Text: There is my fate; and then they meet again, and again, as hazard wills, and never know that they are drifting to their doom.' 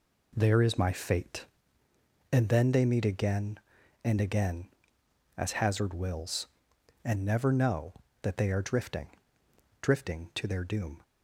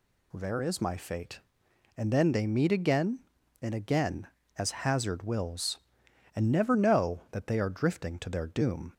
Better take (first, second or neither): second